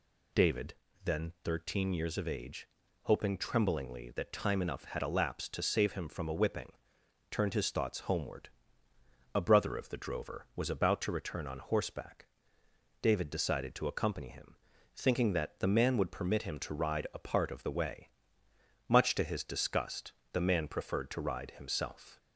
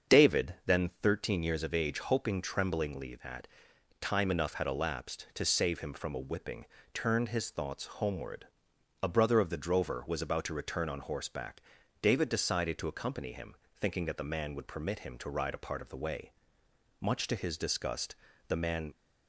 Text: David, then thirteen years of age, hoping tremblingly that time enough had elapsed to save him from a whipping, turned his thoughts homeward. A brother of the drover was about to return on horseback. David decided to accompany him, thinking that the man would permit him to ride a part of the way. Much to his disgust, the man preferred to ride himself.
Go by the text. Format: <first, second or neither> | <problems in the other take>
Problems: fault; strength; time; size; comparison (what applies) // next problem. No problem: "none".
first | starts louder than the rest; until 1.3 s; 7 dB // pauses between "that" and "time"; noticeable; at 3.4 s; 0.54 s long // stops before "preferred to ride himself"; at 18.9 s